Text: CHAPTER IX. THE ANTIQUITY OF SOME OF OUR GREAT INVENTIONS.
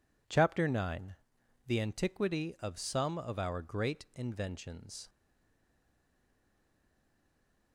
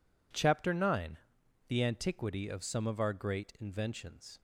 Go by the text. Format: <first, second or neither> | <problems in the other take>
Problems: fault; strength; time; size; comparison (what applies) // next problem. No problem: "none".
second | stays silent after the last word; strong; from 5.0 s on; 2.7 s long